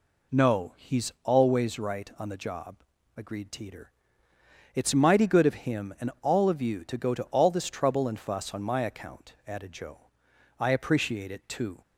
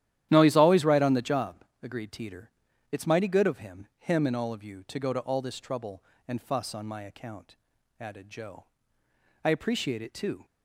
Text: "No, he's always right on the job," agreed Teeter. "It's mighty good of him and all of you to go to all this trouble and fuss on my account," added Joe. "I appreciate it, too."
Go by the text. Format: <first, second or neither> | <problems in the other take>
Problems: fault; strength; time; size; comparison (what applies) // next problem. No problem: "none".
first | starts louder than the rest; strong; until 1.3 s; 12 dB // says "him" twice; at 3.9 s